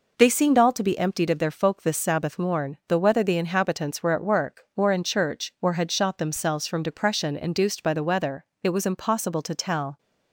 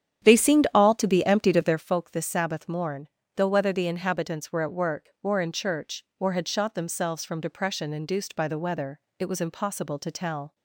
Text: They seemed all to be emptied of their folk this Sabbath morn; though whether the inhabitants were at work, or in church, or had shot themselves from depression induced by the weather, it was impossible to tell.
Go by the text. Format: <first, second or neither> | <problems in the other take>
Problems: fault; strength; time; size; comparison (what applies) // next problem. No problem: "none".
first | starts louder than the rest; strong; until 1.9 s; 9 dB